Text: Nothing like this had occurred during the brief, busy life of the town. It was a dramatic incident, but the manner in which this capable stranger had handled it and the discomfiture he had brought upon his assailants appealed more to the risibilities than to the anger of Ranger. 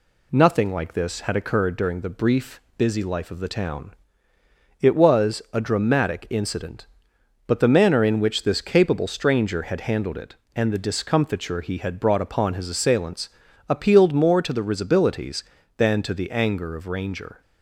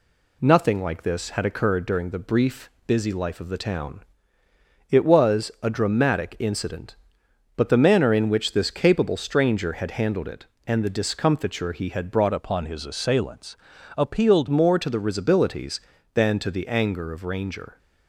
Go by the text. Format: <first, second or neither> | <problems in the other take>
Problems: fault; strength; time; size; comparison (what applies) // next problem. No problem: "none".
first | changes voice from "upon" to "appealed"; from 12.3 to 14.4 s; 2.1 s long // pauses between "assailants" and "appealed"; at 13.5 s; 0.44 s long; also in the first